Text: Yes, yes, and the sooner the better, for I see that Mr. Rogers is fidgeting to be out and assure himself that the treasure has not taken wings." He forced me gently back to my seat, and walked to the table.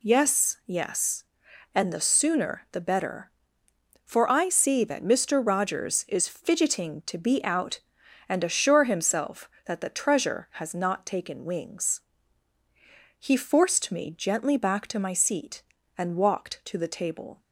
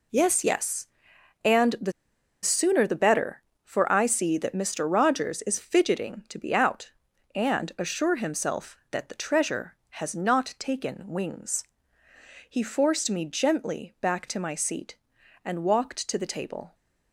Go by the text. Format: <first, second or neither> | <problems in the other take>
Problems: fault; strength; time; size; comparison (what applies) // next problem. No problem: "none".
first | pauses between "the" and "sooner"; noticeable; at 1.9 s; 0.51 s long